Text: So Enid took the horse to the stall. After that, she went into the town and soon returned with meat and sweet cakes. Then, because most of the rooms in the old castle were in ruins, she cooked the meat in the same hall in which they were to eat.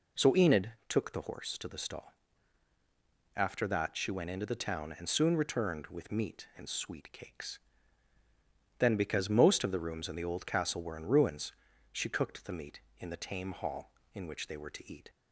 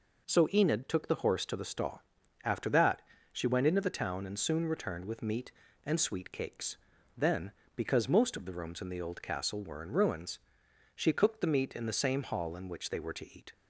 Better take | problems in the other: second | pauses between "Enid" and "took"; slight; at 0.7 s; 0.18 s long // says "tame" for "same"; at 13.1 s

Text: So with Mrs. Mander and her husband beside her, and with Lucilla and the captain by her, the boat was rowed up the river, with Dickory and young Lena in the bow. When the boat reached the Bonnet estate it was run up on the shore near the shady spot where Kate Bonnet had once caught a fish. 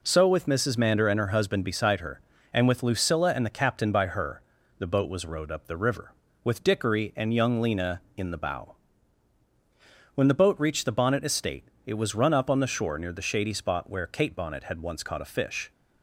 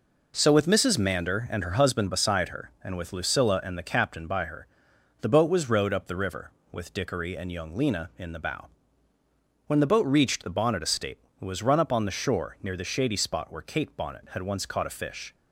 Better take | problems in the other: neither | pauses between "estate" and "it"; slight; the same in both

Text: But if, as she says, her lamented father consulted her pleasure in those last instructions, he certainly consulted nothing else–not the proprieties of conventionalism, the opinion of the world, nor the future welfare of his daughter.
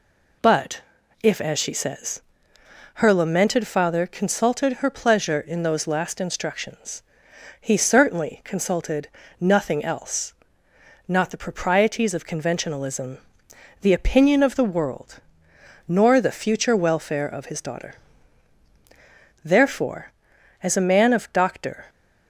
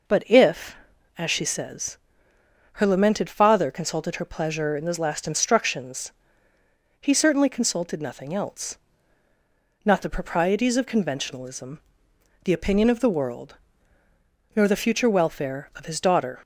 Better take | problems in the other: second | pauses between "But" and "if"; at 0.8 s; 0.42 s long // pauses between "consulted" and "nothing"; slight; at 9.0 s; 0.30 s long // goes on to say "Therefore as a man of Doctor"; strong; from 19.4 s on; 2.4 s long

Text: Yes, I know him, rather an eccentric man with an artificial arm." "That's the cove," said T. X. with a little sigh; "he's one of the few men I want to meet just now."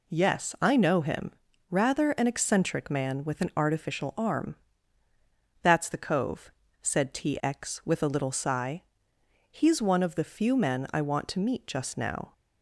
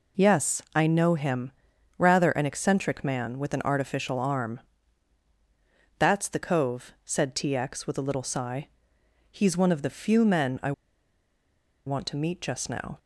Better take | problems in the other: first | pauses between "I" and "want"; at 10.7 s; 1.1 s long

